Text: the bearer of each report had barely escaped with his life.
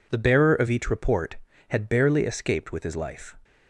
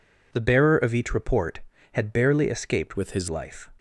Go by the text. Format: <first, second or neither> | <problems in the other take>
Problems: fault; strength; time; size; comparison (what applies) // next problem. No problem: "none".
first | changes voice from "with" to "his"; from 2.9 to 3.2 s; 0.3 s long